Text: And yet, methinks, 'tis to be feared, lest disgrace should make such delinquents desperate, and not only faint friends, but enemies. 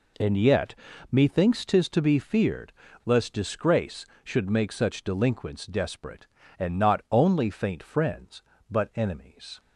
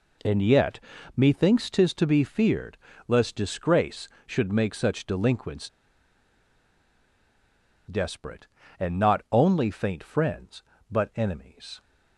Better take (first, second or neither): first